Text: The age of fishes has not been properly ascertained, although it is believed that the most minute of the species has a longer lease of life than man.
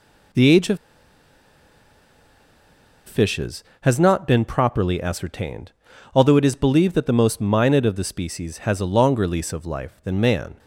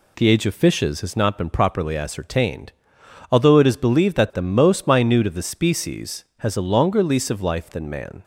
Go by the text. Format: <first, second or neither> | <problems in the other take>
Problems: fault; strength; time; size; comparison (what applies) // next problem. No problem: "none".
second | pauses between "of" and "fishes"; strong; at 0.7 s; 2.2 s long